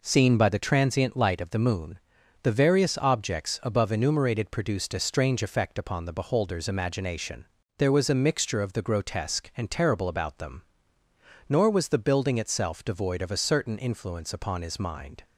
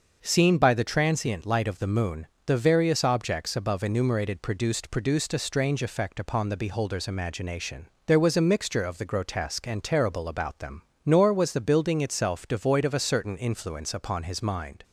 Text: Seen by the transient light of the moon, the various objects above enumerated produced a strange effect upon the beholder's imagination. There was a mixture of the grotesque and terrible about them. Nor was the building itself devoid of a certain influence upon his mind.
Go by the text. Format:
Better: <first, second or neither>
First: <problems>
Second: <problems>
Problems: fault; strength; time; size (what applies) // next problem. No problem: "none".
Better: first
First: none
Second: starts louder than the rest; until 1.2 s; 6 dB // says "produced" twice; at 4.9 s